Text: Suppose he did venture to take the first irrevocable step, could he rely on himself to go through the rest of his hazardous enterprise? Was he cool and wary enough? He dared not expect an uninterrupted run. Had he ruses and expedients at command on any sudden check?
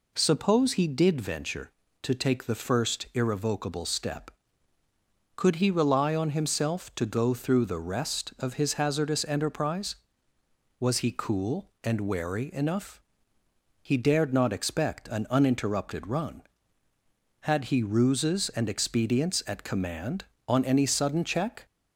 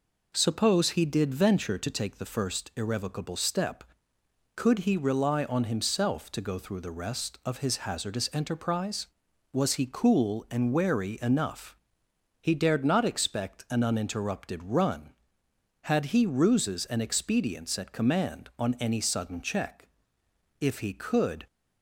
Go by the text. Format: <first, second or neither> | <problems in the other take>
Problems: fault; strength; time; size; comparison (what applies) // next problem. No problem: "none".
first | goes on to say "If he could"; noticeable; from 20.6 s on; 0.86 s long